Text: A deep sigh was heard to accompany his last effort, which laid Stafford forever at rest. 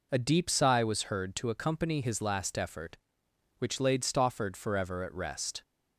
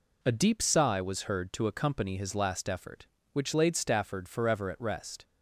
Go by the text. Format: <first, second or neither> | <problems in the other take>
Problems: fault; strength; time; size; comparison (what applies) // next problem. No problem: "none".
neither | none